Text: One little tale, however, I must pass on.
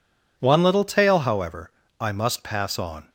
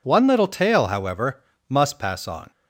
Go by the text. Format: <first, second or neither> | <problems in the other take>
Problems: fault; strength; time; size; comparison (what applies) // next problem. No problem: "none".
first | skips "I"; at 1.5 s